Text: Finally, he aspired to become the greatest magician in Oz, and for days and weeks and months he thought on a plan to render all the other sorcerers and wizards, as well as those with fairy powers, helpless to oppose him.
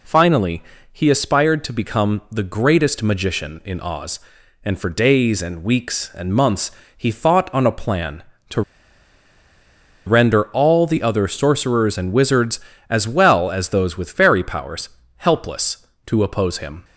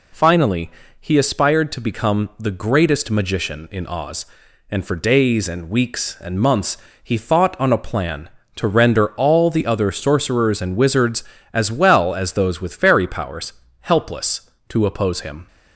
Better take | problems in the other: second | pauses between "months" and "he"; slight; at 6.6 s; 0.26 s long; slight in the second // pauses between "to" and "render"; strong; at 8.6 s; 1.4 s long

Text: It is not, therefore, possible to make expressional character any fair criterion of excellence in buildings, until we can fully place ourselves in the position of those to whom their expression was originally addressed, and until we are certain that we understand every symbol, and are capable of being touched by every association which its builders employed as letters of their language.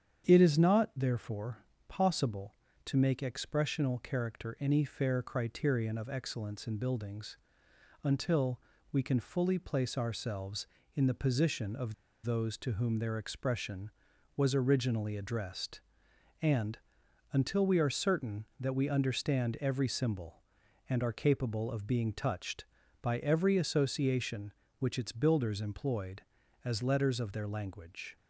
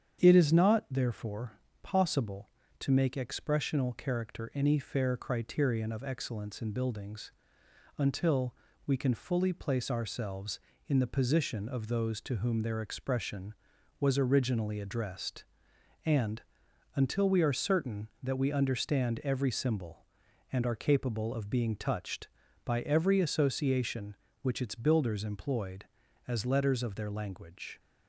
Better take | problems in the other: second | starts louder than the rest; strong; until 1.3 s; 8.5 dB; strong in the second // pauses between "until" and "we"; slight; at 8.5 s; 0.32 s long; slight in the second // pauses between "of" and "those"; slight; at 11.9 s; 0.30 s long // pauses between "and" and "until"; noticeable; at 16.7 s; 0.54 s long; noticeable in the second

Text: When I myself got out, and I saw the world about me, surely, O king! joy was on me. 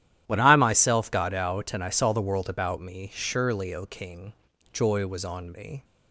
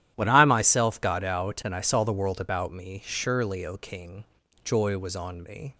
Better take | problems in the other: neither | starts louder than the rest; strong; the same in both

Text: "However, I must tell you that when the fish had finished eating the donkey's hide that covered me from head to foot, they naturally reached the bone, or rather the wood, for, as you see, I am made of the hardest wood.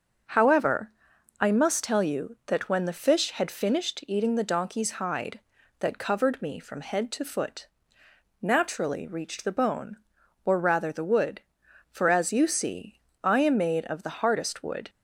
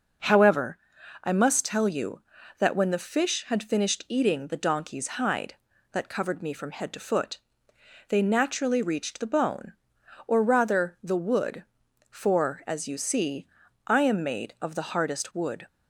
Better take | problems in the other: second | starts louder than the rest; until 1.7 s; 7 dB // skips "they"; at 8.0 s

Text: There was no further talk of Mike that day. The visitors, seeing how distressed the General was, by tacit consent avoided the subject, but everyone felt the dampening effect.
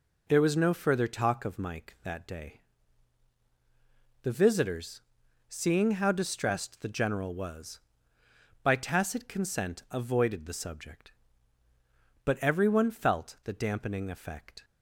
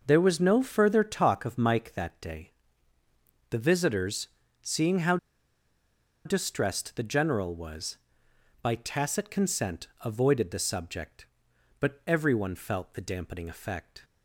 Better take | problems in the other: first | pauses between "how" and "distressed"; at 5.1 s; 1.0 s long // pauses between "consent" and "avoided"; slight; at 9.8 s; 0.18 s long

